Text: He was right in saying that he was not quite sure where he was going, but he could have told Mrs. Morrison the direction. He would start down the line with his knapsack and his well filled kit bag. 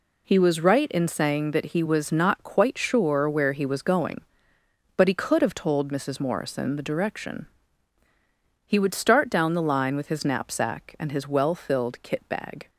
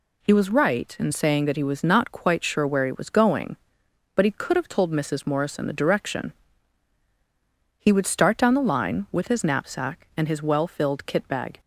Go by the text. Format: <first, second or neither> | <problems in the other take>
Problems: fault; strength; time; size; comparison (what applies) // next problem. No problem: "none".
neither | none